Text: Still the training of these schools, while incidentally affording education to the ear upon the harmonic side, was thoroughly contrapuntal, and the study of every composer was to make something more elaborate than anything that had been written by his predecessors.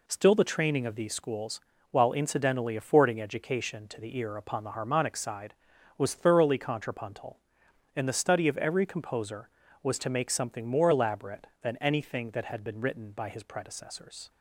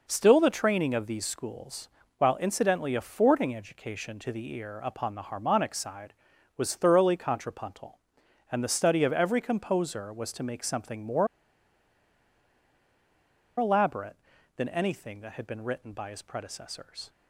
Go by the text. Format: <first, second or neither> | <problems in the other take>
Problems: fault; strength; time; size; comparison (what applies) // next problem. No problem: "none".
first | pauses between "more" and "elaborate"; strong; at 11.2 s; 2.3 s long